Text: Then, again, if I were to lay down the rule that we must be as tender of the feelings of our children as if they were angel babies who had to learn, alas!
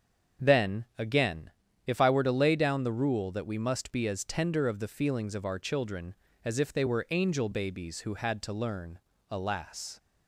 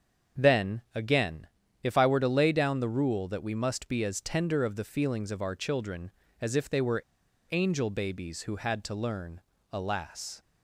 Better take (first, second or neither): first